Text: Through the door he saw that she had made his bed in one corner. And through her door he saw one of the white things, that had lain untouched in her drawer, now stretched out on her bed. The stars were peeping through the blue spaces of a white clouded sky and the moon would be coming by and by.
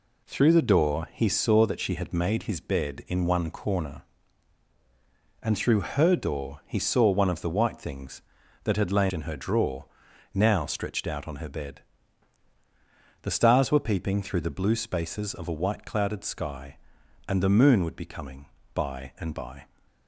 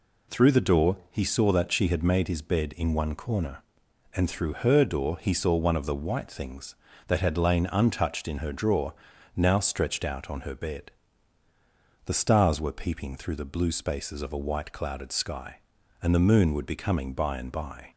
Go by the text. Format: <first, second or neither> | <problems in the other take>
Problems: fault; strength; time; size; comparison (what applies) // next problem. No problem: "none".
second | skips "untouched"; at 9.1 s